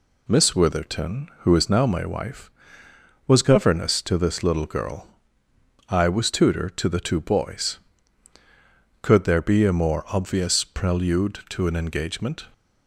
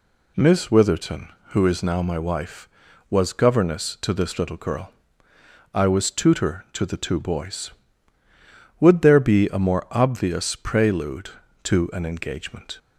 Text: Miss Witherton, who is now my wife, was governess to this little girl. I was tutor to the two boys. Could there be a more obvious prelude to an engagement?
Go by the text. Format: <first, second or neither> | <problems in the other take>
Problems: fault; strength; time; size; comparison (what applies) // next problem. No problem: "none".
first | says "Would" for "Could"; at 8.8 s